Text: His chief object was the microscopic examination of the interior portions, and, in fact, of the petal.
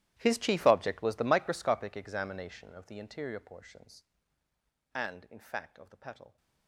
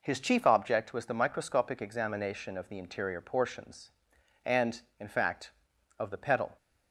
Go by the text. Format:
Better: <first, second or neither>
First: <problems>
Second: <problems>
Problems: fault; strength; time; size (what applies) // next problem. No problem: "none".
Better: second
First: gets quieter; strong; throughout; 22 dB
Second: none